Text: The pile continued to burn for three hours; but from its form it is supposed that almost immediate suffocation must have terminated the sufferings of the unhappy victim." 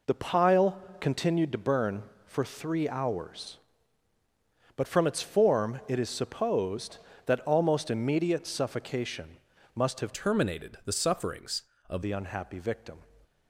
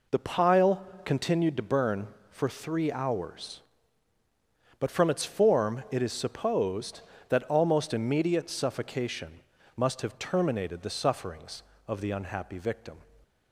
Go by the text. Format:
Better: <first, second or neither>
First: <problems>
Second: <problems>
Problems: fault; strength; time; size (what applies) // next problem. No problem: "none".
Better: second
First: pauses between "pile" and "continued"; slight; at 0.7 s; 0.22 s long // pauses between "suffocation" and "must"; at 9.3 s; 0.38 s long // changes voice from "terminated" to "of"; from 10.1 to 12.0 s; 1.9 s long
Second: pauses between "pile" and "continued"; slight; at 0.8 s; 0.22 s long // pauses between "suffocation" and "must"; at 9.3 s; 0.37 s long